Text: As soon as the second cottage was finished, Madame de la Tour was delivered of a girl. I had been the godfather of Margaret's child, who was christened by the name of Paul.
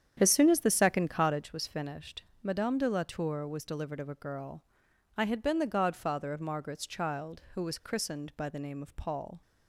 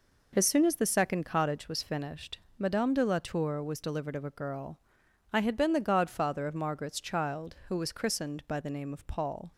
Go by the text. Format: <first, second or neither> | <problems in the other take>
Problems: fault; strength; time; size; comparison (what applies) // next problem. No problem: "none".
second | starts louder than the rest; strong; until 1.5 s; 8.5 dB